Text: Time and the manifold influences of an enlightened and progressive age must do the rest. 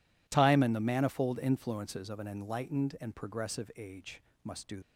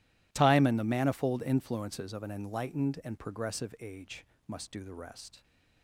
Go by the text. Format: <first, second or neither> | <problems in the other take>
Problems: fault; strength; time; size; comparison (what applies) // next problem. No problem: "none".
second | pauses between "age" and "must"; slight; at 4.2 s; 0.22 s long; slight in the second // stops before "the rest"; at 4.8 s